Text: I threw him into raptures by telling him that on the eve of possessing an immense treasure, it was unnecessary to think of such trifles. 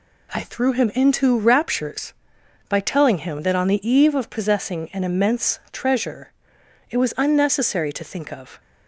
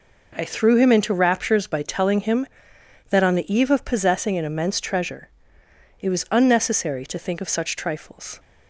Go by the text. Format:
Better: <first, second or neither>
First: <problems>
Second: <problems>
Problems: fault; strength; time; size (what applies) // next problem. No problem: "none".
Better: second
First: stops before "such trifles"; at 8.5 s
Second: none